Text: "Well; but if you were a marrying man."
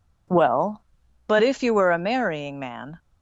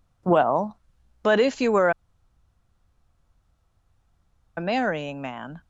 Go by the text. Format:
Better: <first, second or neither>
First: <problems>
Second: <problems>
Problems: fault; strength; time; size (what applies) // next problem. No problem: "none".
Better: first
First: none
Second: pauses between "were" and "a"; strong; at 1.9 s; 2.6 s long